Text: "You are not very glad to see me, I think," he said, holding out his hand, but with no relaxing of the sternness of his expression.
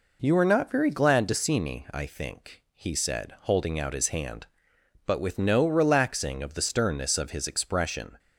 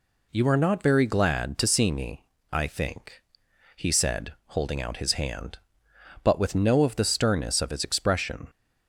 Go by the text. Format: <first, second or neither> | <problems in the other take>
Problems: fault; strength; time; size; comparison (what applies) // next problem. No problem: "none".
first | skips "relaxing"; at 6.8 s